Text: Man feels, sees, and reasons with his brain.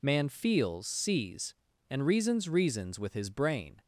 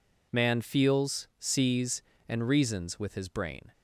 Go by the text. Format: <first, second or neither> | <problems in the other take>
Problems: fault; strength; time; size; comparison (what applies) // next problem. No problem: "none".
second | says "reasons" twice; at 2.4 s